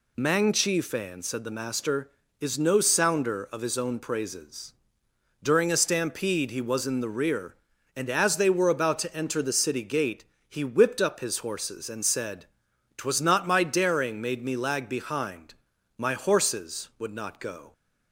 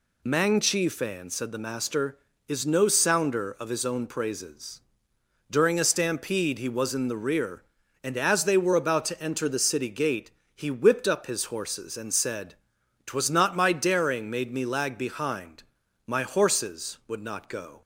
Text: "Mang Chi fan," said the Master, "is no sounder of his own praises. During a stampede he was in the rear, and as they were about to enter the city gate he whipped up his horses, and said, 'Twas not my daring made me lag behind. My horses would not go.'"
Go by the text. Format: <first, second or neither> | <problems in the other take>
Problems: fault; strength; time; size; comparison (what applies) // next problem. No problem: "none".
neither | pauses between "gate" and "he"; slight; the same in both